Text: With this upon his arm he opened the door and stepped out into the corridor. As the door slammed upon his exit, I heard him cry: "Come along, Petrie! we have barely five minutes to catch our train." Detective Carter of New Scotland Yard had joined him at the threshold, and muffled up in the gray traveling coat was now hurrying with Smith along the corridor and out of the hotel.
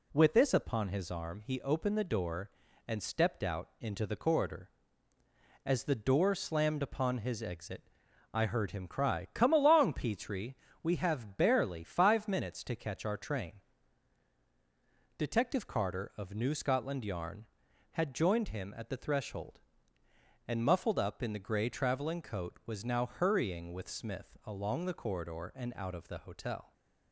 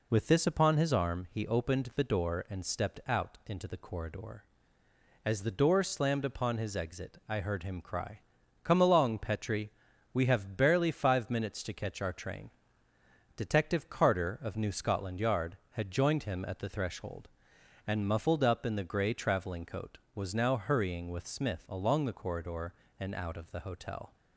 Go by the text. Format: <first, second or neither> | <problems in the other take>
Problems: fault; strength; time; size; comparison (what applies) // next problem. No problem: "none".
second | says "Yarn" for "Yard"; at 17.0 s